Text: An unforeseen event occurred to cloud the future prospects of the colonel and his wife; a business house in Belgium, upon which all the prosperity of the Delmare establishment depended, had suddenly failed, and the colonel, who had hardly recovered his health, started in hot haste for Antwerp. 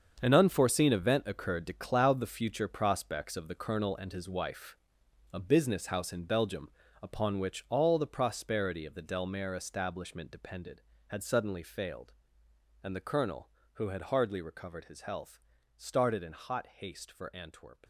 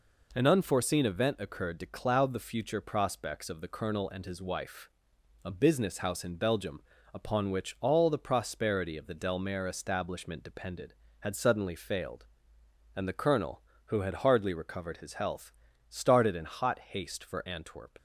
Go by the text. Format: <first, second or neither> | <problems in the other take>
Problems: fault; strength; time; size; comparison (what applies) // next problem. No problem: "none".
second | gets quieter; strong; throughout; 11.5 dB